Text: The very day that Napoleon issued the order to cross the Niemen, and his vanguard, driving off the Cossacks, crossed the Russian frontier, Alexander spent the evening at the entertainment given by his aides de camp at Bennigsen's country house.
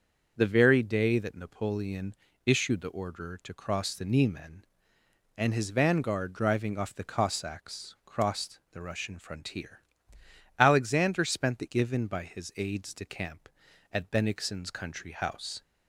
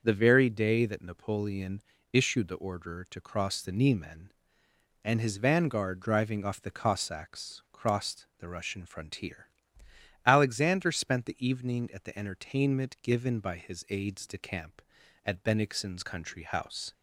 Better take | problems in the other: second | starts louder than the rest; until 1.3 s; 6.5 dB; also in the second // pauses between "Napoleon" and "issued"; slight; at 2.1 s; 0.32 s long; slight in the second // skips "evening at the entertainment"; at 11.6 s

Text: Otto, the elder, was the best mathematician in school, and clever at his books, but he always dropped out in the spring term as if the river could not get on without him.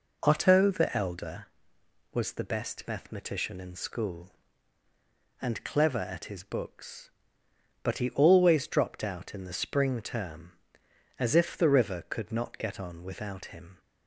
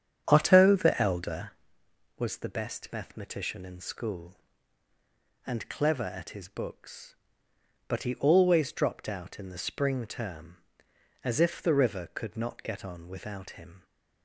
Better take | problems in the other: first | starts louder than the rest; strong; until 1.7 s; 8.5 dB

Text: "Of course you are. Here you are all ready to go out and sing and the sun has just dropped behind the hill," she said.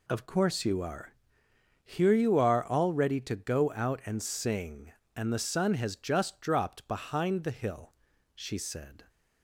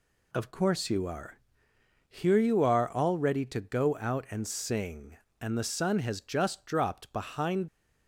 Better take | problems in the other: first | stops before "the hill she said"; at 7.6 s

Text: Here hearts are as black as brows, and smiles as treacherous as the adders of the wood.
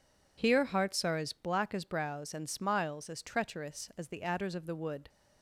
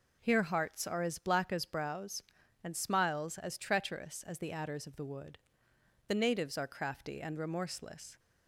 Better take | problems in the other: first | goes on to say "The natives are crafty and remorseless"; strong; from 6.0 s on; 2.1 s long

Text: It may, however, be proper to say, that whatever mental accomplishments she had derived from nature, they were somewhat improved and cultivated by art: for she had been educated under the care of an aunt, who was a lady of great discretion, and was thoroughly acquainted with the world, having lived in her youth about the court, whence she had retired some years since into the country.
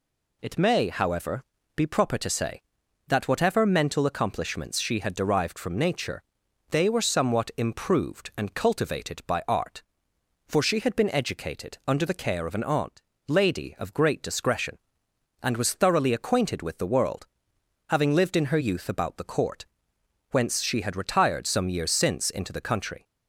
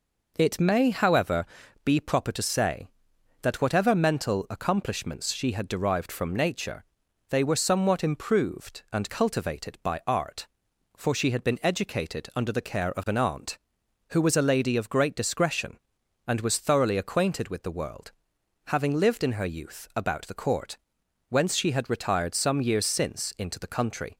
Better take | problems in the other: second | skips "who was a"; at 13.1 s

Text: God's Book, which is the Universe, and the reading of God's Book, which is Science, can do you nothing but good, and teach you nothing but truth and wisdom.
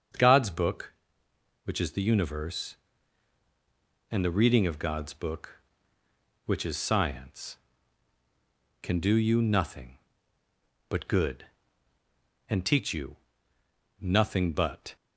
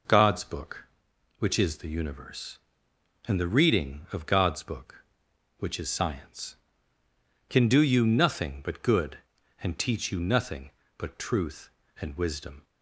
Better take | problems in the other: second | starts louder than the rest; until 1.8 s; 6.5 dB // pauses between "you" and "nothing"; noticeable; at 13.1 s; 0.86 s long // stops before "truth and wisdom"; at 14.9 s

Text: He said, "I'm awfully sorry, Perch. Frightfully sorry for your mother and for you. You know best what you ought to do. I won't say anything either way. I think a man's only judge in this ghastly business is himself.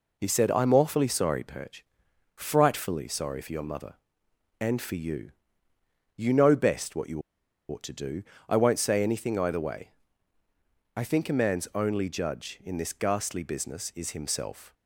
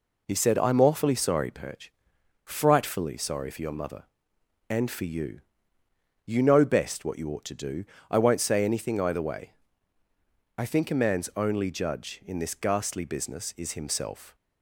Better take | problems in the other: second | pauses between "you" and "ought"; noticeable; at 7.2 s; 0.47 s long

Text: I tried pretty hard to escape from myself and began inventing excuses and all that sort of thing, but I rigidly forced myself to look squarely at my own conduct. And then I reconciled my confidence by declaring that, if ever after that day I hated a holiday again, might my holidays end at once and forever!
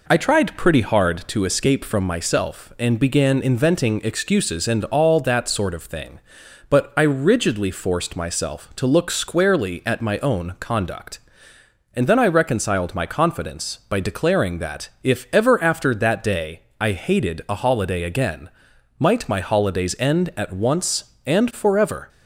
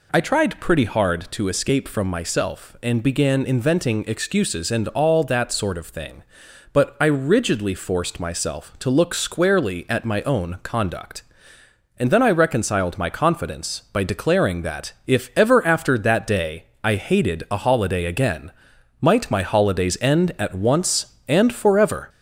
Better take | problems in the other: first | gets louder; slight; throughout; 2.5 dB // pauses between "day" and "I"; slight; at 16.6 s; 0.18 s long; slight in the first

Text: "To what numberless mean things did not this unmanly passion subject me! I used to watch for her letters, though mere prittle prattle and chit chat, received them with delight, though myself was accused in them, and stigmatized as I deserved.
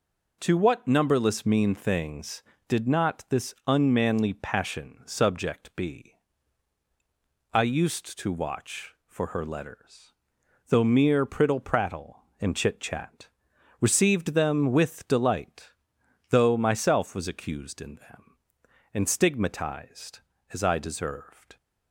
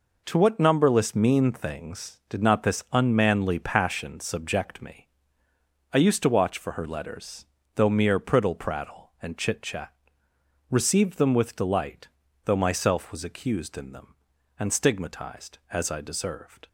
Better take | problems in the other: second | says "be" for "me"; at 5.7 s

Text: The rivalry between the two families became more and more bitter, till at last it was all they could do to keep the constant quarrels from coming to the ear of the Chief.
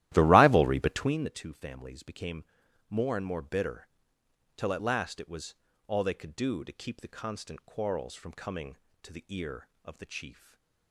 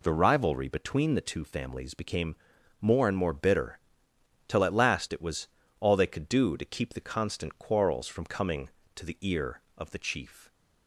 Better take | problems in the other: second | starts louder than the rest; strong; until 1.2 s; 14.5 dB // pauses between "became" and "more"; noticeable; at 2.4 s; 0.46 s long; noticeable in the second // pauses between "was" and "all"; slight; at 5.5 s; 0.32 s long; slight in the second // stays silent after the last word; slight; from 10.3 s on; 0.6 s long

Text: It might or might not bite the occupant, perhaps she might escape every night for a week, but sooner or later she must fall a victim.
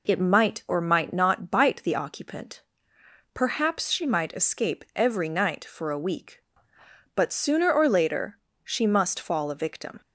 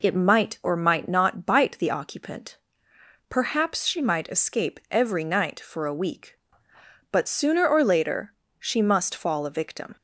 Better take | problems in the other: neither | pauses between "later" and "she"; slight; the same in both

